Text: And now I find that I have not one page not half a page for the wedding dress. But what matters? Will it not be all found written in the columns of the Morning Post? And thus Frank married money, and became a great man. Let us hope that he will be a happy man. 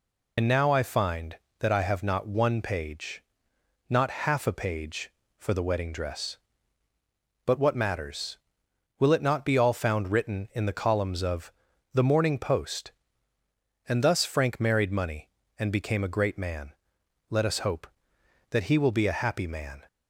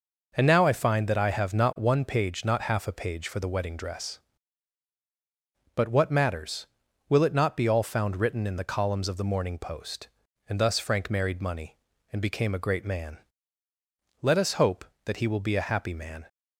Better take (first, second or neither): second